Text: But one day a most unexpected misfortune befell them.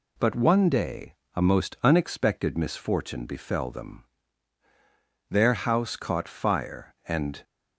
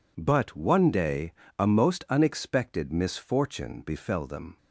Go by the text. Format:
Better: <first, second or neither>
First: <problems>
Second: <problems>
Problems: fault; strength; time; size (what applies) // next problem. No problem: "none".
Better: second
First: pauses between "day" and "a"; slight; at 1.1 s; 0.22 s long // goes on to say "Their house caught fire and"; strong; from 5.2 s on; 2.1 s long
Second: pauses between "day" and "a"; slight; at 1.3 s; 0.24 s long